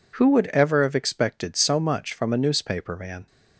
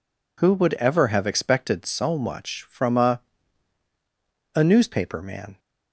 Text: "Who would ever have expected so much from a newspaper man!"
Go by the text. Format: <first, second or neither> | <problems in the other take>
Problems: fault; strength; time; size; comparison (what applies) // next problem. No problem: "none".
first | says "a" twice; at 4.5 s